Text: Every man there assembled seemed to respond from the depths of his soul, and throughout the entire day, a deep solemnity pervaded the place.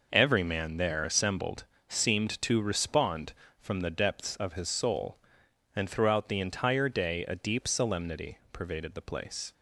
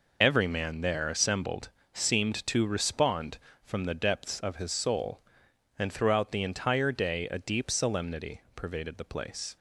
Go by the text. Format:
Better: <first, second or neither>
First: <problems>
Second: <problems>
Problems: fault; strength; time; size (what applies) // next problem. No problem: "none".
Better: first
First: pauses between "assembled" and "seemed"; slight; at 1.6 s; 0.24 s long // pauses between "solemnity" and "pervaded"; slight; at 8.3 s; 0.16 s long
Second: loses the start of "Every"; at 0.2 s; 45 ms // pauses between "assembled" and "seemed"; slight; at 1.6 s; 0.24 s long // pauses between "solemnity" and "pervaded"; slight; at 8.3 s; 0.16 s long